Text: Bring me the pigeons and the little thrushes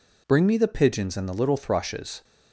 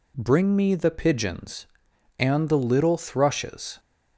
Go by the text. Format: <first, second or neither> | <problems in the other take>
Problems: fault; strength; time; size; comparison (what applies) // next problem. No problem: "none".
neither | none